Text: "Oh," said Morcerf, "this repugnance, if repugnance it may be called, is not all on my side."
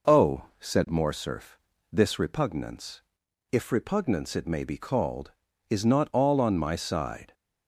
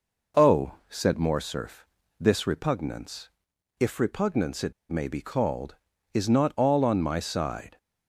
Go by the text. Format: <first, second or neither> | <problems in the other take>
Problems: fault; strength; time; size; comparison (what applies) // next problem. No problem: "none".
first | pauses between "it" and "may"; slight; at 4.7 s; 0.18 s long